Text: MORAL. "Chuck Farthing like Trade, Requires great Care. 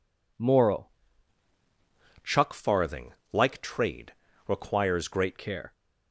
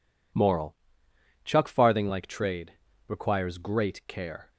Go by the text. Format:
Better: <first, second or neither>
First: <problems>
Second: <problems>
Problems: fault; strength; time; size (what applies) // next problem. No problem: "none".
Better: second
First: changes voice from "Chuck" to "great"; from 2.2 to 5.3 s; 3.1 s long // pauses between "Farthing" and "like"; slight; at 3.1 s; 0.20 s long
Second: none